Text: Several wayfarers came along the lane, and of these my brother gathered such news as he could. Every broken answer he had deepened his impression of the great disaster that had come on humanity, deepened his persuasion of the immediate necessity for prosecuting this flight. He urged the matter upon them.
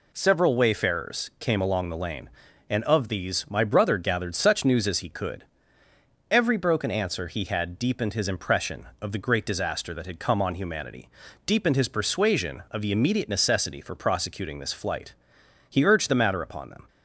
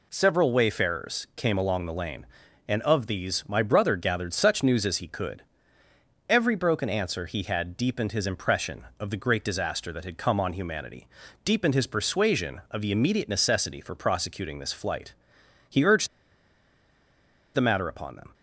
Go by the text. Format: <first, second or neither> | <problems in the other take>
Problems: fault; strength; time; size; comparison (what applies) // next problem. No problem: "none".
first | pauses between "urged" and "the"; strong; at 16.0 s; 1.4 s long